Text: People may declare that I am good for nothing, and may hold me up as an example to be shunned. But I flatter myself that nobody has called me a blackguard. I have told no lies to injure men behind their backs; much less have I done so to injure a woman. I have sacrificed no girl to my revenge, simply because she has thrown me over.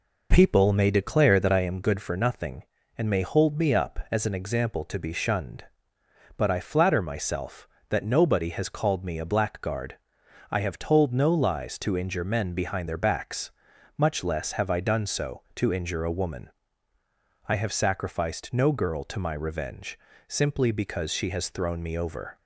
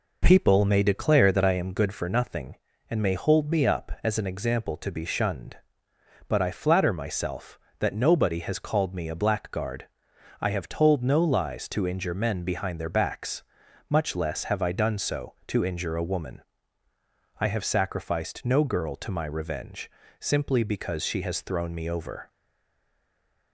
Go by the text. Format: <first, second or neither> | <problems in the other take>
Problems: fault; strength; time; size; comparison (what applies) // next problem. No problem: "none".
first | stays silent after the last word; noticeable; from 22.2 s on; 1.3 s long